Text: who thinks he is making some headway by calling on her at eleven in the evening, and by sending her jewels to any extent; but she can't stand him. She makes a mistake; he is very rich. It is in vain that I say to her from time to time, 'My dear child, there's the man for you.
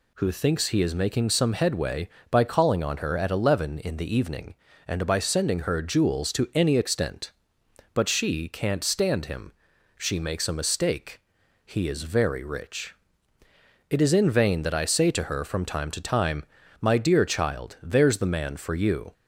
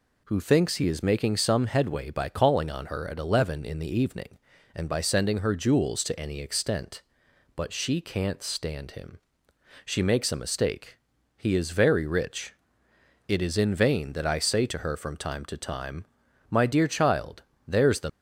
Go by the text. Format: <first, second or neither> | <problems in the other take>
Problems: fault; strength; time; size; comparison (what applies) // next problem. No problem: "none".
first | stops before "man for you"; at 18.0 s